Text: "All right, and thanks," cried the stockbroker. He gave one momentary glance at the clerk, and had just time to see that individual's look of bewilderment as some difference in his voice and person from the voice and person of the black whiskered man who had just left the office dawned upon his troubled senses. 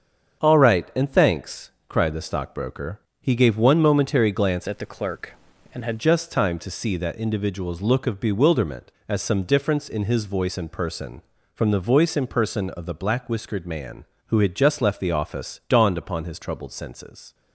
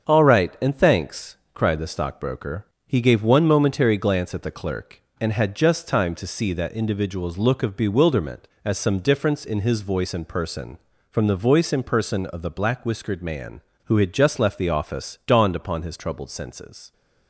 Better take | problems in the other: second | starts louder than the rest; strong; until 1.4 s; 7 dB; strong in the second // changes voice from "at" to "had"; from 4.6 to 5.9 s; 1.3 s long

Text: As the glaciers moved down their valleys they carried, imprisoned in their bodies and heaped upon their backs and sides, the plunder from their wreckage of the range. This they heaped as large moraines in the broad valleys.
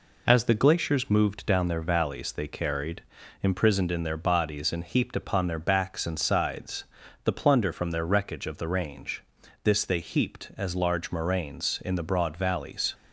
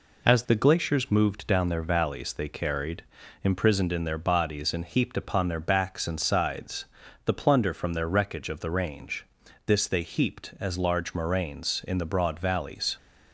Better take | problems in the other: neither | none

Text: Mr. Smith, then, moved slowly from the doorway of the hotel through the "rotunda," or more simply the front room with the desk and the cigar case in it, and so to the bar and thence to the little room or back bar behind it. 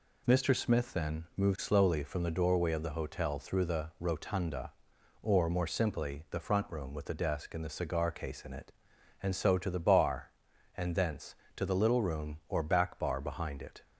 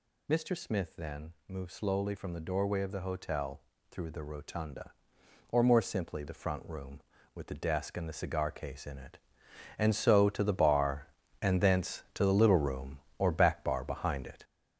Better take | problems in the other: first | gets louder; throughout; 6.5 dB // pauses between "hotel" and "through"; slight; at 3.6 s; 0.28 s long

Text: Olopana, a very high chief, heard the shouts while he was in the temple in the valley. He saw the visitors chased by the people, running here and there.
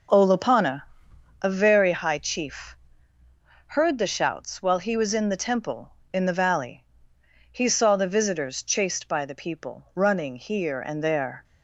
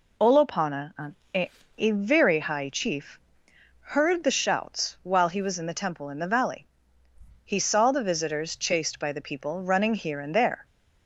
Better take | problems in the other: first | says "a" twice; at 1.7 s

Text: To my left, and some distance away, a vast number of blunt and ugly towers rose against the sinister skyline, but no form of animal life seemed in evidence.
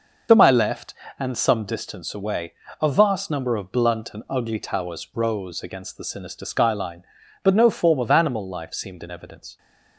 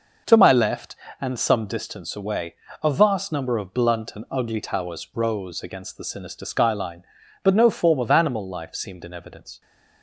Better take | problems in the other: second | loses the start of "To"; at 0.2 s; 45 ms

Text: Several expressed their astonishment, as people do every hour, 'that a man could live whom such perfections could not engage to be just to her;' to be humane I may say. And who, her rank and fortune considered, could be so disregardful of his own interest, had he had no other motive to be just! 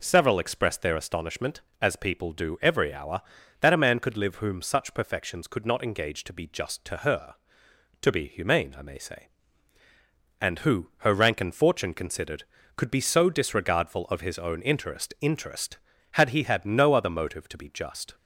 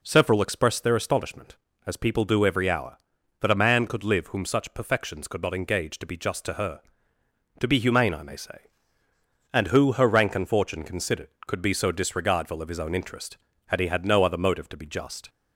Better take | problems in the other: second | says "interest" twice; at 15.2 s

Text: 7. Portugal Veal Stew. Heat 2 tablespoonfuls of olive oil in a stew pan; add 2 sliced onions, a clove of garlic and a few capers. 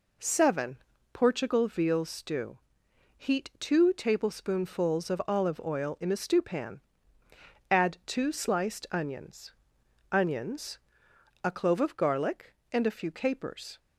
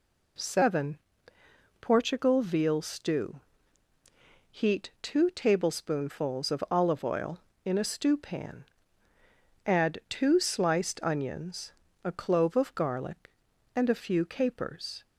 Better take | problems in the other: second | says "onions" twice; at 10.1 s

